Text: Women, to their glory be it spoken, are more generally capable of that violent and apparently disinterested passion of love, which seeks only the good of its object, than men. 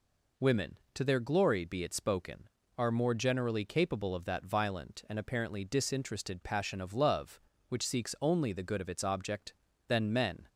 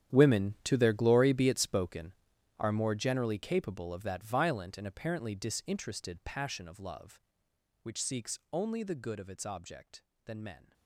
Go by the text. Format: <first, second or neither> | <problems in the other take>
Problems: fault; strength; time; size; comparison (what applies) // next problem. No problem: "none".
first | gets quieter; strong; throughout; 17 dB